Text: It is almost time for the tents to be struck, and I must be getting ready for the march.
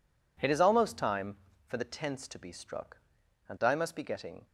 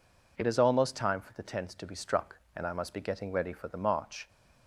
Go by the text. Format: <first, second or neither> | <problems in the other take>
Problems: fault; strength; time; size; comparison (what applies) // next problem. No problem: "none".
second | stops before "ready for the march"; at 4.4 s